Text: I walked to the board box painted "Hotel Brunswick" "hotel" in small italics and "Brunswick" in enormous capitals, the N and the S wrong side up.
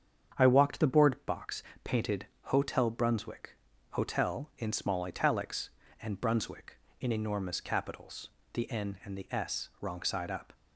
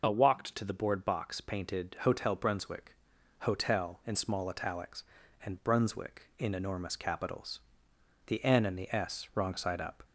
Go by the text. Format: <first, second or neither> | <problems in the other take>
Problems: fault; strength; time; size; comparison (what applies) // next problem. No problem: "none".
second | starts louder than the rest; strong; until 1.4 s; 7.5 dB // skips "to"; at 0.7 s // pauses between "box" and "painted"; slight; at 1.6 s; 0.20 s long // pauses between "painted" and "Hotel"; slight; at 2.2 s; 0.20 s long // pauses between "Brunswick" and "hotel"; slight; at 3.5 s; 0.36 s long; also in the second